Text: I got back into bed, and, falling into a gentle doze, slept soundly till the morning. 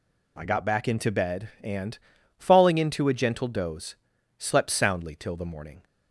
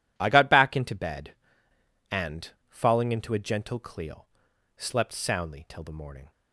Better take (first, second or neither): first